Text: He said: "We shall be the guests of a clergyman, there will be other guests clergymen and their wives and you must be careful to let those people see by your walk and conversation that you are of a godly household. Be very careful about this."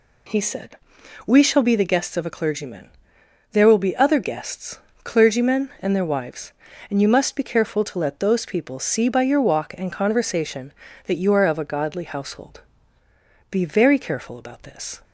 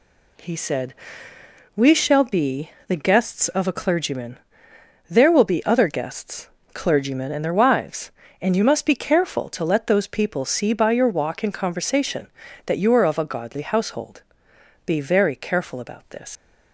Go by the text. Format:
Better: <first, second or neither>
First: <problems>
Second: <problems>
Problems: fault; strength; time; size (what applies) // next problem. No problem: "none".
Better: first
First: pauses between "guests" and "clergymen"; slight; at 4.7 s; 0.28 s long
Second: pauses between "be" and "the"; slight; at 2.7 s; 0.16 s long // pauses between "guests" and "clergymen"; slight; at 6.4 s; 0.24 s long // leaves "this" unfinished; at 16.3 s; 100 ms